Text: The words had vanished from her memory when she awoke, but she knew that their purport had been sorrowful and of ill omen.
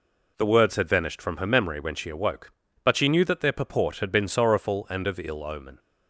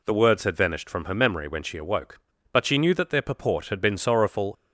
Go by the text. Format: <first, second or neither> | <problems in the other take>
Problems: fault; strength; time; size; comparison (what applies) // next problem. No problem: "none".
first | stops before "and of ill omen"; at 4.5 s